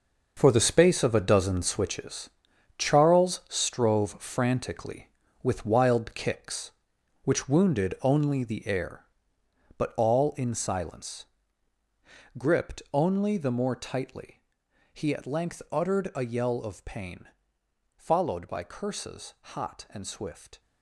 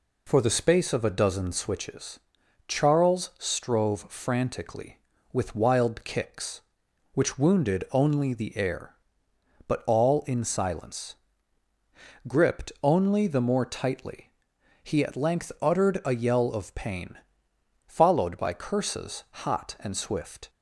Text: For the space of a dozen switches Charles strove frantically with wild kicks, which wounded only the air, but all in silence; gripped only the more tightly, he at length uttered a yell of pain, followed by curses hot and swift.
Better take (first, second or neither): second